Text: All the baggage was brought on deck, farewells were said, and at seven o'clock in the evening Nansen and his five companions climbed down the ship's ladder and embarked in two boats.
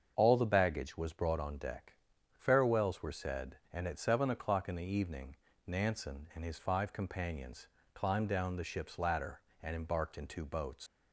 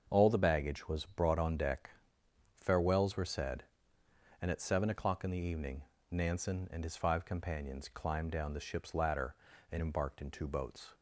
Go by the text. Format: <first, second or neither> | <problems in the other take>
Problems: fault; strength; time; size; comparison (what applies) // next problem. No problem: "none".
second | starts louder than the rest; until 1.1 s; 7 dB; also in the second // pauses between "evening" and "Nansen"; slight; at 5.3 s; 0.28 s long; slight in the second // pauses between "companions" and "climbed"; slight; at 7.6 s; 0.26 s long // leaves "boats" unfinished; at 10.8 s; 95 ms